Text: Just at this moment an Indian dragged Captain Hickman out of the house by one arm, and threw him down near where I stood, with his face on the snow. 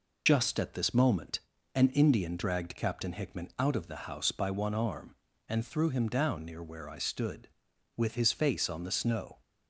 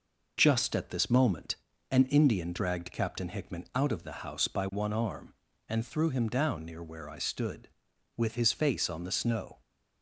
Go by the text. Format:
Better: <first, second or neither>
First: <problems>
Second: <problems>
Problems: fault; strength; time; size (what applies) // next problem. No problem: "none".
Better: second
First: loses the start of "Just"; at 0.2 s; 40 ms // pauses between "moment" and "an"; slight; at 1.4 s; 0.34 s long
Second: pauses between "moment" and "an"; slight; at 1.5 s; 0.34 s long